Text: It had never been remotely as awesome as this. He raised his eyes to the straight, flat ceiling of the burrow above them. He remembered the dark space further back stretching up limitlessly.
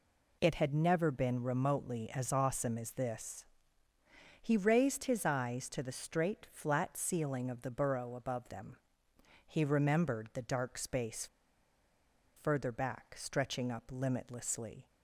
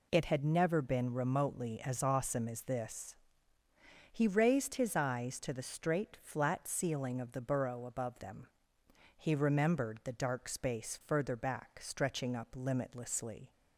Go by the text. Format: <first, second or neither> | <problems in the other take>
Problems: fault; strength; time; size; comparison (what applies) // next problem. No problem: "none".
second | pauses between "space" and "further"; at 11.2 s; 1.1 s long